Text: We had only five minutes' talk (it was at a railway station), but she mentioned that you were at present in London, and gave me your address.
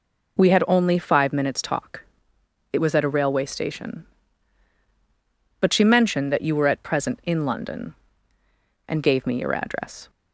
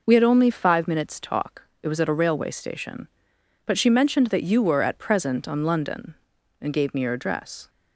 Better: first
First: none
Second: says "on" for "in"; at 5.4 s

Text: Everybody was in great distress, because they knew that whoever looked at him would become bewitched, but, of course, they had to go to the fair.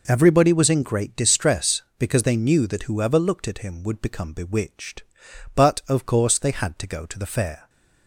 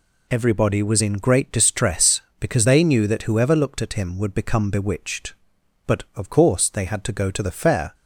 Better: neither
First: none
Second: none

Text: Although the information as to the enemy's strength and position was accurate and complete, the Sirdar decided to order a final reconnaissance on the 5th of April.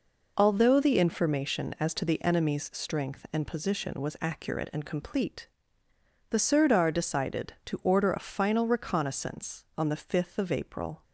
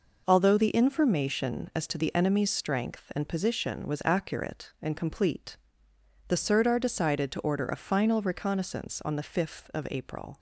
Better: neither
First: none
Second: none

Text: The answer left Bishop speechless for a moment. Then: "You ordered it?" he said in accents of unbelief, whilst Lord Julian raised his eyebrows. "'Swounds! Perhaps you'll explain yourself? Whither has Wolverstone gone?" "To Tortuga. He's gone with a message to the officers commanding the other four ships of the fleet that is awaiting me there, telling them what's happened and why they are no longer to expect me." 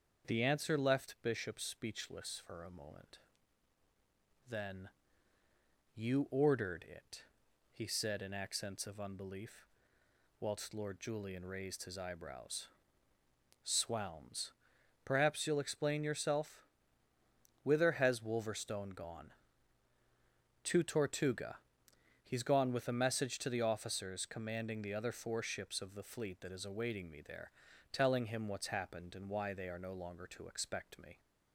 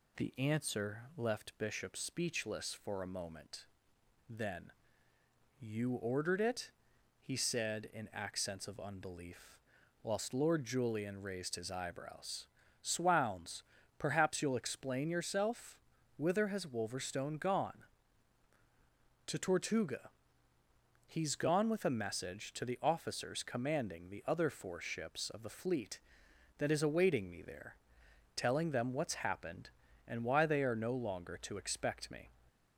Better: second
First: starts louder than the rest; until 1.3 s; 6.5 dB // says "him" for "them"; at 28.2 s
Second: none

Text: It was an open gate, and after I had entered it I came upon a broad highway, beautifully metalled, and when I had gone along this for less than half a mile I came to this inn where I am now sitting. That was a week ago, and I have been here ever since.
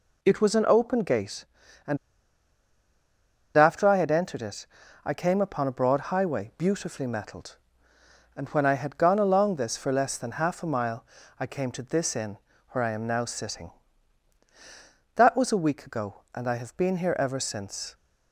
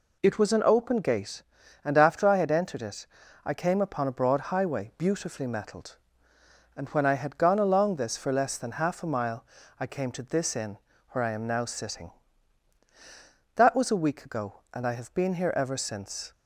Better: second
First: pauses between "and" and "after"; strong; at 1.9 s; 1.5 s long // pauses between "it" and "I"; at 4.6 s; 0.38 s long // pauses between "mile" and "I"; slight; at 11.0 s; 0.34 s long // pauses between "inn" and "where"; slight; at 12.3 s; 0.32 s long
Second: pauses between "it" and "I"; at 3.0 s; 0.38 s long // pauses between "mile" and "I"; slight; at 9.4 s; 0.34 s long // pauses between "inn" and "where"; slight; at 10.7 s; 0.32 s long

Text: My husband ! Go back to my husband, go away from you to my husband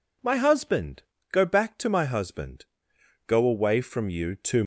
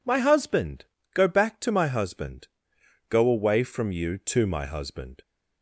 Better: second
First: stops before "my husband"; at 4.6 s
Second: none

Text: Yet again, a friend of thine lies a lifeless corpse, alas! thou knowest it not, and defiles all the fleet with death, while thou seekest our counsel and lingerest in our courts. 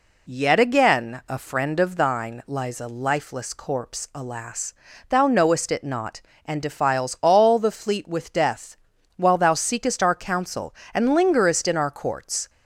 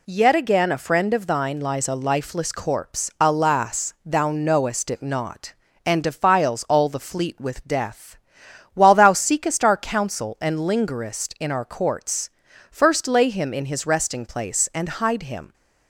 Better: first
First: none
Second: goes on to say "First lay him in his resting place and hide him"; strong; from 12.7 s on; 2.8 s long

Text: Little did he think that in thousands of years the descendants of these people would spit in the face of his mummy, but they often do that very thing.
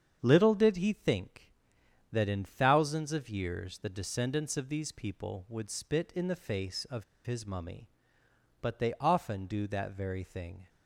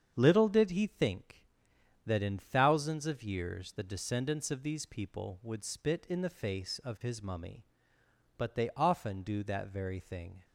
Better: second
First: starts louder than the rest; strong; until 1.2 s; 7.5 dB // pauses between "of" and "his"; slight; at 7.0 s; 0.22 s long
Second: starts louder than the rest; strong; until 1.1 s; 7.5 dB

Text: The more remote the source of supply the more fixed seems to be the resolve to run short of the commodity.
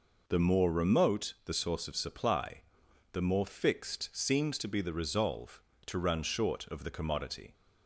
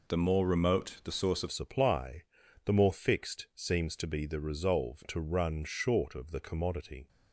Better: first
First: pauses between "supply" and "the"; noticeable; at 2.6 s; 0.50 s long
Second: changes voice at "supply"; from 1.4 s on; 5.6 s long // pauses between "supply" and "the"; at 2.2 s; 0.40 s long

